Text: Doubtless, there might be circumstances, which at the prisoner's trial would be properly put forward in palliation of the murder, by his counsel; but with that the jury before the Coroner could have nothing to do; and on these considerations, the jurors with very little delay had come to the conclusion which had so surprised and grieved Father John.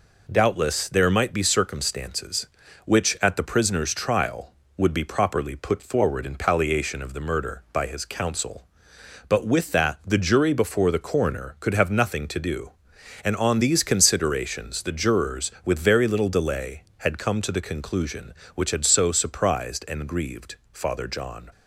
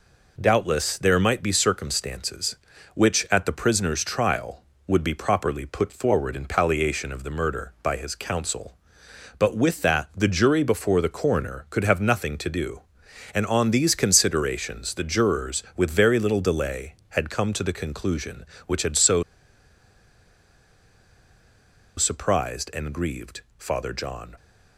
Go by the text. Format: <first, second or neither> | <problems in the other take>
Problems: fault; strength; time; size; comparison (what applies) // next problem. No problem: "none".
first | pauses between "so" and "surprised"; strong; at 19.2 s; 2.7 s long // pauses between "grieved" and "Father"; slight; at 23.3 s; 0.18 s long; slight in the first